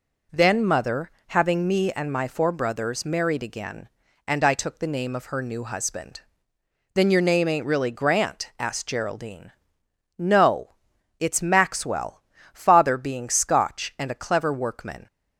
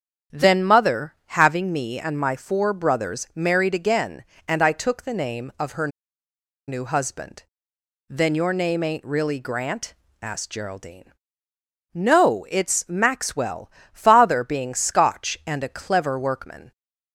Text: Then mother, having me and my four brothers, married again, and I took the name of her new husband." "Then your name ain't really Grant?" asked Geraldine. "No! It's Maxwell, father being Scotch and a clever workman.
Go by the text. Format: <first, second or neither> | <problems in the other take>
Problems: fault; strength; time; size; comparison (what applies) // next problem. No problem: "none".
first | starts louder than the rest; strong; until 1.4 s; 8 dB // pauses between "her" and "new"; noticeable; at 5.8 s; 0.79 s long